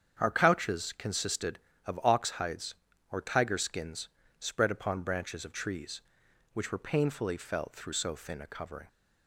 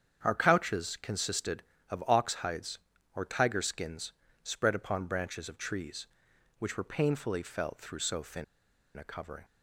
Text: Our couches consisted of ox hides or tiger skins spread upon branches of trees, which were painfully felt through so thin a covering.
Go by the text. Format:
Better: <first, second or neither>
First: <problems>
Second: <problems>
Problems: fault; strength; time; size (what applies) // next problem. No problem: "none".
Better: first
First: starts louder than the rest; strong; until 1.2 s; 8 dB // pauses between "skins" and "spread"; slight; at 4.0 s; 0.32 s long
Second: starts louder than the rest; strong; until 1.2 s; 8 dB // pauses between "skins" and "spread"; slight; at 4.1 s; 0.32 s long // pauses between "thin" and "a"; noticeable; at 8.4 s; 0.53 s long